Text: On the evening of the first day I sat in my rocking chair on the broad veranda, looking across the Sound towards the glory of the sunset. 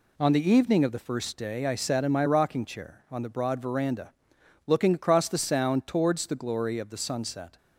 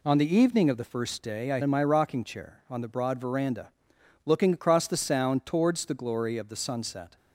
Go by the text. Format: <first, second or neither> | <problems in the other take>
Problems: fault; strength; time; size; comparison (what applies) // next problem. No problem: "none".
first | skips "sat"; at 1.6 s